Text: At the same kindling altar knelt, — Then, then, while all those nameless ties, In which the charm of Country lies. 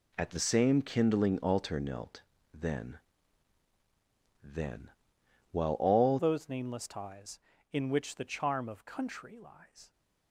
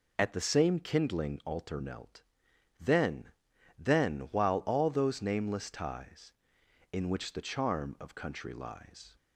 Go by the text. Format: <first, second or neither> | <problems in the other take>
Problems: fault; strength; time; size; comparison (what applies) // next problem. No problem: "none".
second | changes voice at "those"; from 6.1 s on; 3.8 s long